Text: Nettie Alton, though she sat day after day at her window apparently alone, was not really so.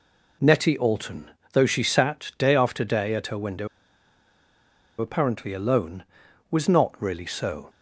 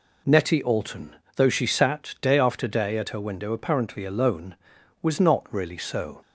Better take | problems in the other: second | pauses between "window" and "apparently"; strong; at 3.6 s; 1.3 s long

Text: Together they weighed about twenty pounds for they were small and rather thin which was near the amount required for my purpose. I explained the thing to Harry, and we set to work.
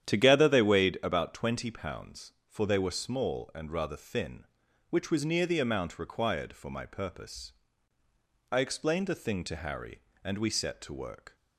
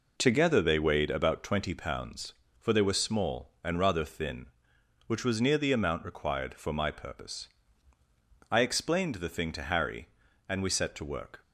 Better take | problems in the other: second | starts louder than the rest; strong; until 1.2 s; 10 dB

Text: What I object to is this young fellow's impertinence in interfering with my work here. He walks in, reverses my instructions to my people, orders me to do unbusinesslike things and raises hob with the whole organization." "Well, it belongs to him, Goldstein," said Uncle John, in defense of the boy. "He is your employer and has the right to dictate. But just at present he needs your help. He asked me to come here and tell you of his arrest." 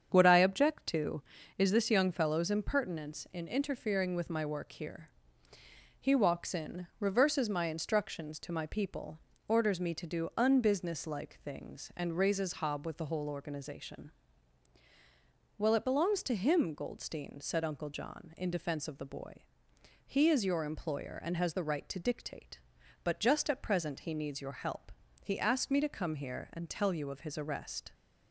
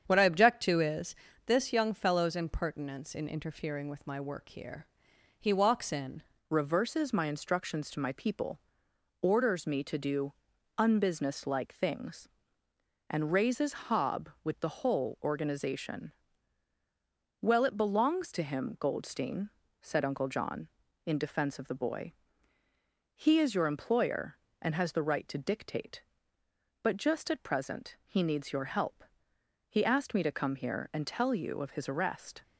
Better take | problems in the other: first | starts louder than the rest; strong; until 1.0 s; 7.5 dB; strong in the first // pauses between "is" and "this"; slight; at 1.1 s; 0.32 s long // changes voice at "reverses"; from 6.5 s on; 25.9 s long // pauses between "do" and "unbusinesslike"; noticeable; at 10.3 s; 0.46 s long

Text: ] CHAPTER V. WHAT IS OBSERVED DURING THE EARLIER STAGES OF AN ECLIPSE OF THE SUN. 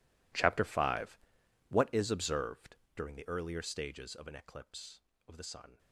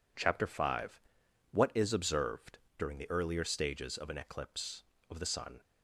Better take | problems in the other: second | gets quieter; strong; throughout; 19 dB // pauses between "OBSERVED" and "DURING"; slight; at 2.7 s; 0.20 s long; slight in the second

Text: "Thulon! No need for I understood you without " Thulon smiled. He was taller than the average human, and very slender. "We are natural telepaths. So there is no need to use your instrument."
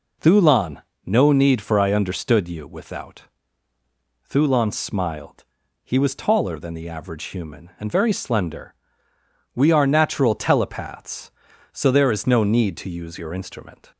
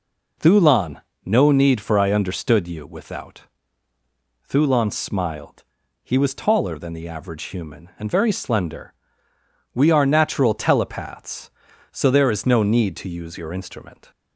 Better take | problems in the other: neither | none

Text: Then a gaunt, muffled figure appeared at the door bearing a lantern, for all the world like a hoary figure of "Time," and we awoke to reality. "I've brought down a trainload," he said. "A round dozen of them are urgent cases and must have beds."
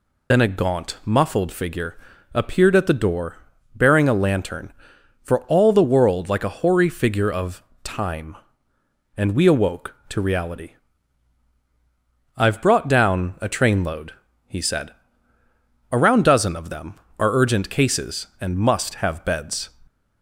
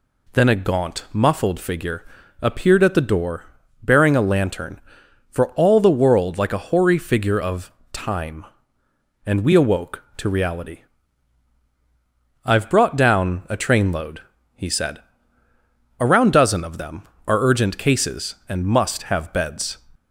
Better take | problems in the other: second | loses the start of "Then"; at 0.3 s; 95 ms // pauses between "figure" and "appeared"; at 1.9 s; 0.38 s long; also in the second // pauses between "door" and "bearing"; at 3.3 s; 0.38 s long; also in the second // pauses between "of" and "Time"; slight; at 7.6 s; 0.22 s long; slight in the second

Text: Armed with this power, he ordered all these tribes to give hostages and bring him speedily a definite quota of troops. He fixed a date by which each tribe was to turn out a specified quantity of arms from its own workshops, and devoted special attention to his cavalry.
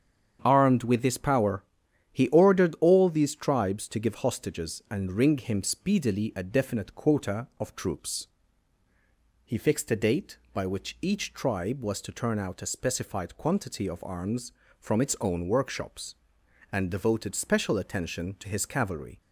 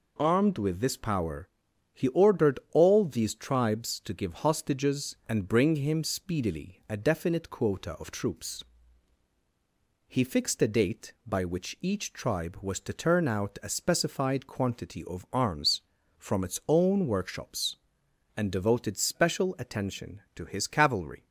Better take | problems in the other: second | starts louder than the rest; strong; until 1.4 s; 8 dB // says "ring" for "bring"; at 5.1 s

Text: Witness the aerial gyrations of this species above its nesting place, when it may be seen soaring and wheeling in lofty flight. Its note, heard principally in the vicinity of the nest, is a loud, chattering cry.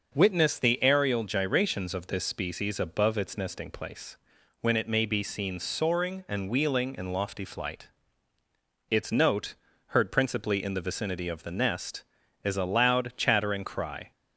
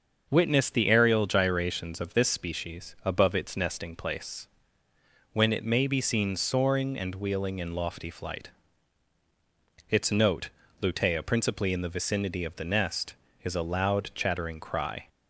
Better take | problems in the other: first | starts louder than the rest; until 1.3 s; 6.5 dB // says "lutea" for "heard"; at 10.7 s

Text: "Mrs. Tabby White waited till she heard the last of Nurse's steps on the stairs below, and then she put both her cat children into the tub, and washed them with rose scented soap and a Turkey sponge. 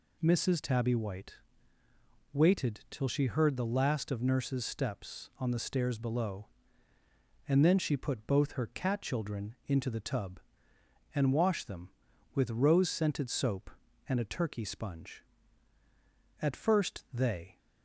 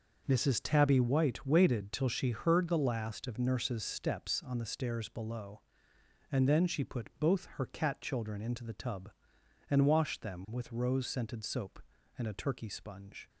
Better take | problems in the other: second | pauses between "White" and "waited"; noticeable; at 1.3 s; 0.98 s long // goes on to say "At first they"; noticeable; from 16.4 s on; 1.1 s long

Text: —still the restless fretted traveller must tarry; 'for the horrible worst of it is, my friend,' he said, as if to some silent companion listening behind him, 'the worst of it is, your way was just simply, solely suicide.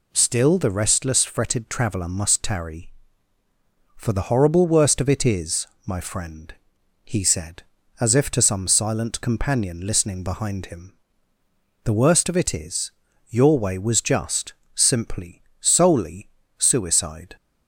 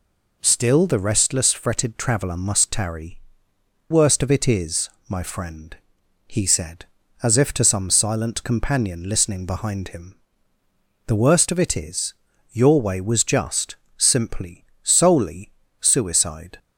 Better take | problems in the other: first | skips "for the horrible"; at 3.5 s // pauses between "just" and "simply"; slight; at 13.7 s; 0.20 s long; slight in the first // pauses between "solely" and "suicide"; slight; at 15.5 s; 0.30 s long; slight in the first

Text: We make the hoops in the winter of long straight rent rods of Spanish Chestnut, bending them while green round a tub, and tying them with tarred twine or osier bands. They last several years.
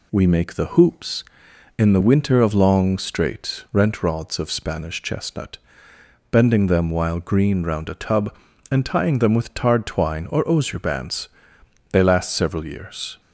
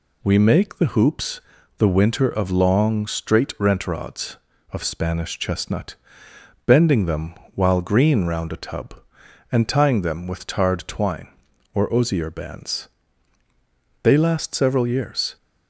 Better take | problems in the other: first | skips "in"; at 1.5 s // pauses between "them" and "while"; slight; at 7.3 s; 0.18 s long

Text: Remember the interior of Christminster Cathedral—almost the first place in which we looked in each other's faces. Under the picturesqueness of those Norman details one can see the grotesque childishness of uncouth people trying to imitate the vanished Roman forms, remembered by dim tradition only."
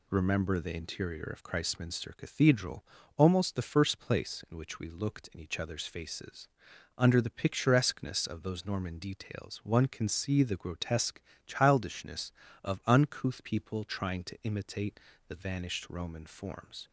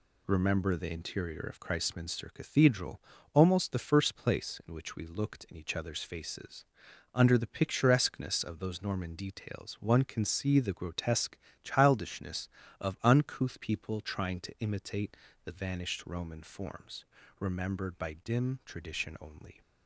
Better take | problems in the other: second | pauses between "grotesque" and "childishness"; slight; at 11.2 s; 0.26 s long; slight in the second // pauses between "imitate" and "the"; slight; at 14.9 s; 0.30 s long; slight in the second // stops before "remembered by dim tradition only"; at 16.8 s

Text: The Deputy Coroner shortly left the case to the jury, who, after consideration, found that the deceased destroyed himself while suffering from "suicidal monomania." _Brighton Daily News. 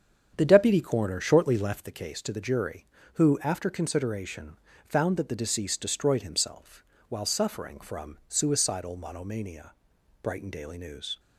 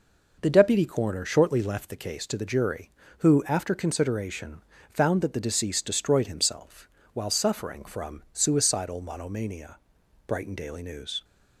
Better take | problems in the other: second | starts louder than the rest; strong; until 1.9 s; 8 dB // pauses between "himself" and "while"; slight; at 6.8 s; 0.24 s long; slight in the second

